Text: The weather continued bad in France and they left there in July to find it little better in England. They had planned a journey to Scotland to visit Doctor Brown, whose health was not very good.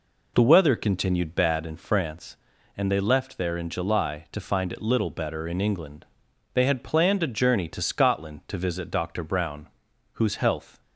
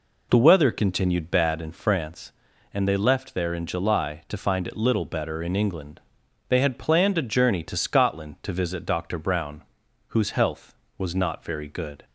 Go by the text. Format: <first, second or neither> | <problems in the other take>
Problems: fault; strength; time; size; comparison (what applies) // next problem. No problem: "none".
second | stops before "was not very good"; at 10.8 s